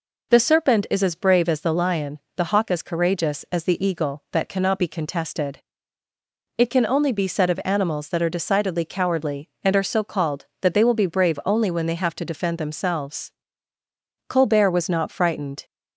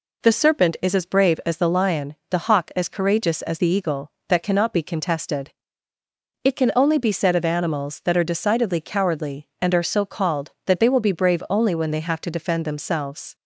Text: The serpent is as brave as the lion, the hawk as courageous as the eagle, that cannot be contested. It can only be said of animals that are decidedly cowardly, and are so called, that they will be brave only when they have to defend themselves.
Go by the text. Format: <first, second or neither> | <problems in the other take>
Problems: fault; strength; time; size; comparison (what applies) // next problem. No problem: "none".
second | goes on to say "Colbert was not frightened"; from 14.2 s on; 1.3 s long